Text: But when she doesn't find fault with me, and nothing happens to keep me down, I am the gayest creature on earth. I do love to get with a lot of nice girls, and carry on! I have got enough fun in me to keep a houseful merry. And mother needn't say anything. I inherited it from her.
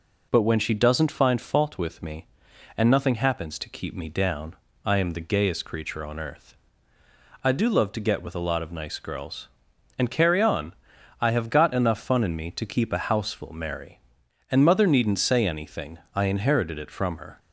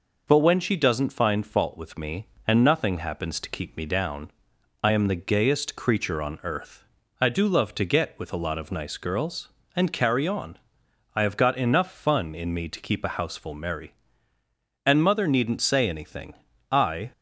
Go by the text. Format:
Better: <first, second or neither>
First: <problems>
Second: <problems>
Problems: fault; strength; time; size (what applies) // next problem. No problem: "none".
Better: first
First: none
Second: stops before "inherited it from her"; at 17.1 s